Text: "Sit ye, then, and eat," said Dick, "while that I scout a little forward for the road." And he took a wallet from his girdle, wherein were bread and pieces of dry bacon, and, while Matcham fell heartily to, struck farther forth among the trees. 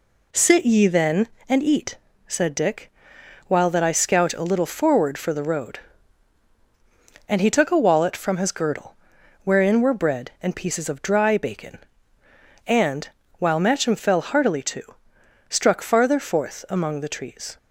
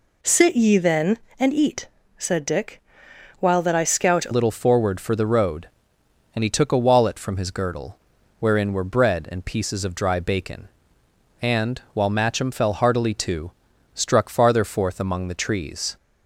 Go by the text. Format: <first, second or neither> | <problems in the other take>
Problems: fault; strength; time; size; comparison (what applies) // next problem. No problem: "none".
first | changes voice at "little"; from 4.3 s on; 11.6 s long